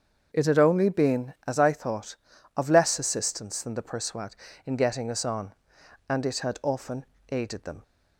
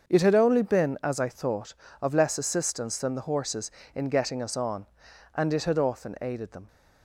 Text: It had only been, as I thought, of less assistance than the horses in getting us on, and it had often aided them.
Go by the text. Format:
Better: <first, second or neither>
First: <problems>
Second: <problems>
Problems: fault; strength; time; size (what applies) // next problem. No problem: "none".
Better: second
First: starts louder than the rest; until 1.3 s; 6.5 dB // says "persuad" for "horses"; at 3.8 s // pauses between "often" and "aided"; slight; at 7.0 s; 0.26 s long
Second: starts louder than the rest; until 1.1 s; 6.5 dB